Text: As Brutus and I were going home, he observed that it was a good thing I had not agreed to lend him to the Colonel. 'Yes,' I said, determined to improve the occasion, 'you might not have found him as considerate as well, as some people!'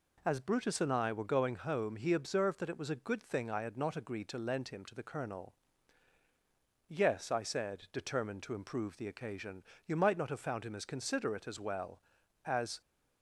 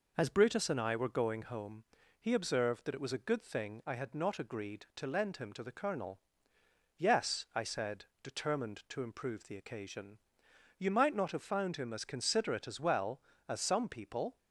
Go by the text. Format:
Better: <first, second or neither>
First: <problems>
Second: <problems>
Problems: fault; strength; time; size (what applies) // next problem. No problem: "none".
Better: second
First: stops before "some people"; at 12.8 s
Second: none